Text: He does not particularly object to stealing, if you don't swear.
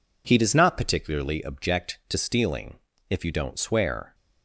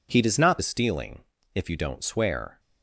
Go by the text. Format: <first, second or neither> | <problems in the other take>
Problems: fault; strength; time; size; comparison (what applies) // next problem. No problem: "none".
first | skips "particularly object to"; at 0.6 s